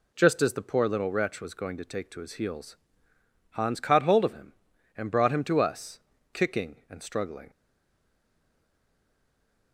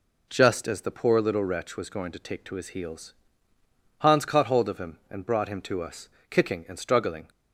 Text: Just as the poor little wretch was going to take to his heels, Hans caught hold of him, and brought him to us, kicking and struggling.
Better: second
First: stays silent after the last word; from 7.5 s on; 2.2 s long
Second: none

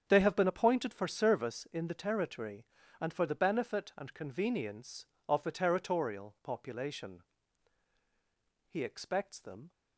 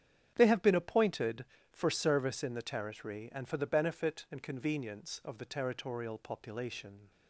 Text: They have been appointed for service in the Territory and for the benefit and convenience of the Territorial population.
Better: second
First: starts louder than the rest; strong; until 1.0 s; 8 dB // goes on to say "He expects them"; noticeable; from 8.6 s on; 1.0 s long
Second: starts louder than the rest; strong; until 1.3 s; 9 dB

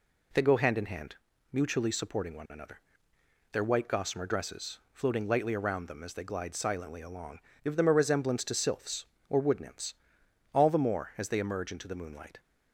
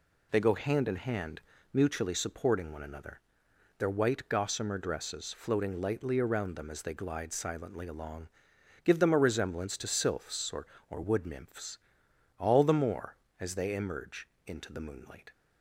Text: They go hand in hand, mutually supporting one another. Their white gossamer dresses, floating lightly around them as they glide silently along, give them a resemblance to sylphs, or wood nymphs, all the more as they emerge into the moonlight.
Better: first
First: none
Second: says "or" twice; at 10.8 s // pauses between "emerge" and "into"; slight; at 14.2 s; 0.18 s long

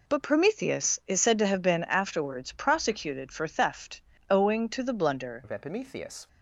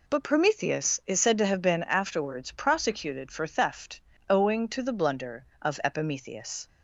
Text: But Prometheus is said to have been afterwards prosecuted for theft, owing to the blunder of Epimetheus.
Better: second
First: changes voice at "of"; from 5.4 s on; 0.8 s long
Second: none

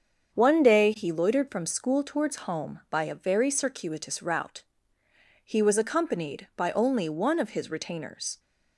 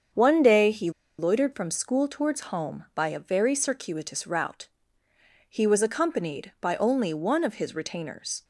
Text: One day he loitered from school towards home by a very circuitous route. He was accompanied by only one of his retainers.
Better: first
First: starts louder than the rest; strong; until 1.3 s; 7.5 dB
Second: starts louder than the rest; strong; until 1.4 s; 7.5 dB // pauses between "he" and "loitered"; slight; at 0.9 s; 0.28 s long

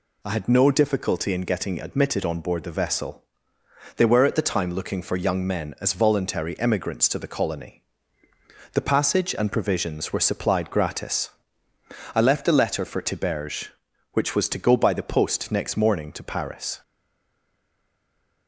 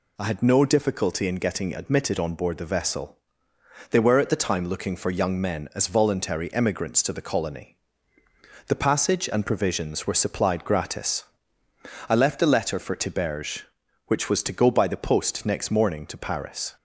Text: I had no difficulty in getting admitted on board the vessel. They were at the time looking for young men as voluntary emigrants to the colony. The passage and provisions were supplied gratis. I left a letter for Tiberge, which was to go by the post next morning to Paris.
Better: second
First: stays silent after the last word; noticeable; from 16.8 s on; 1.6 s long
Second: none

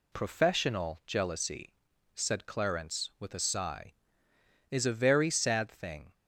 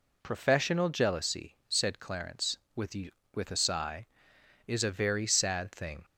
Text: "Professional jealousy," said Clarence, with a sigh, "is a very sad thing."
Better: first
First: none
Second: says "with" twice; at 3.3 s

